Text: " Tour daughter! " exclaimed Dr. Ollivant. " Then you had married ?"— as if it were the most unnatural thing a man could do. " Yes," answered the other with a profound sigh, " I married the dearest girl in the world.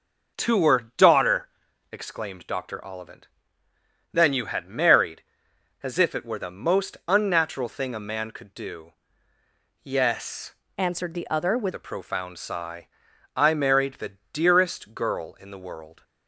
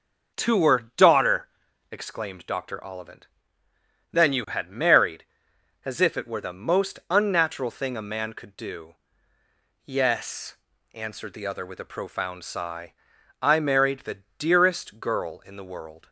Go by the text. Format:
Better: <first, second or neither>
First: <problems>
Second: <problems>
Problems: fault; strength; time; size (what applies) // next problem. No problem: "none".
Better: second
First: changes voice from "answered" to "with"; from 10.7 to 11.7 s; 1.0 s long // pauses between "the" and "dearest"; slight; at 14.1 s; 0.16 s long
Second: pauses between "the" and "dearest"; slight; at 14.2 s; 0.16 s long